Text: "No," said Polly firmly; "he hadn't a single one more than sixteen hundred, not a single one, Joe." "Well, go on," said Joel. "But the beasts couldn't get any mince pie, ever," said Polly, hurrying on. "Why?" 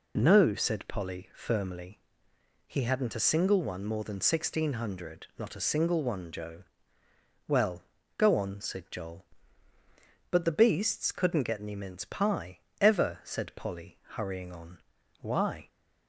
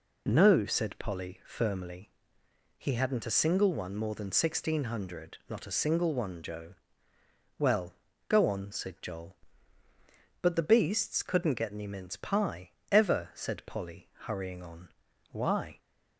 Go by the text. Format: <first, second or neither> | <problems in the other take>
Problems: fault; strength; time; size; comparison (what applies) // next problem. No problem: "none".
neither | none